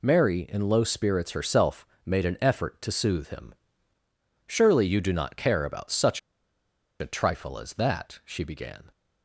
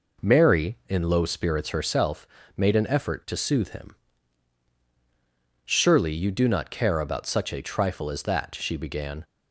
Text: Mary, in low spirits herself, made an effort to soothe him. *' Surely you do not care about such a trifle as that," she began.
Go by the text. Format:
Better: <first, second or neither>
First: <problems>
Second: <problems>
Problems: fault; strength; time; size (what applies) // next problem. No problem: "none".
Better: second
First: pauses between "such" and "a"; noticeable; at 6.1 s; 0.80 s long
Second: none